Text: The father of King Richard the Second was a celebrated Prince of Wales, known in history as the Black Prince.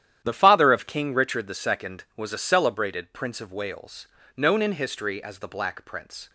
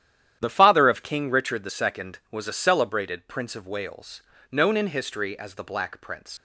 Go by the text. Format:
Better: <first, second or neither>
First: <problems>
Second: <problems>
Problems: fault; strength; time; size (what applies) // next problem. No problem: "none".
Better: first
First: starts louder than the rest; strong; until 1.2 s; 11 dB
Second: starts louder than the rest; strong; until 1.4 s; 10.5 dB // leaves "Prince" unfinished; at 6.3 s; 80 ms